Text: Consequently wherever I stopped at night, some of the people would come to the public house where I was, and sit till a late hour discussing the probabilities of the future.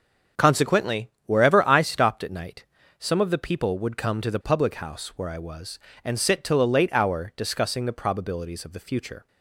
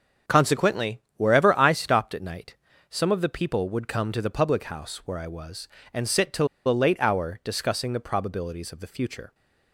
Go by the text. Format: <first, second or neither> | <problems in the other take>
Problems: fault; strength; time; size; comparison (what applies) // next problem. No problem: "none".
first | starts louder than the rest; strong; until 1.4 s; 7 dB; strong in the first // pauses between "Consequently" and "wherever"; slight; at 0.9 s; 0.18 s long; slight in the first // pauses between "till" and "a"; slight; at 6.4 s; 0.20 s long